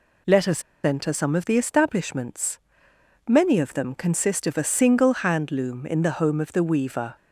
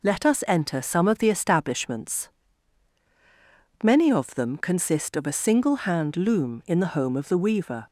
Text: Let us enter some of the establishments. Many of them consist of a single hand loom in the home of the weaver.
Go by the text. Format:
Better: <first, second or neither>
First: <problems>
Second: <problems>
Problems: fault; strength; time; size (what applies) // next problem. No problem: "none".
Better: second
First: pauses between "us" and "enter"; slight; at 0.6 s; 0.23 s long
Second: none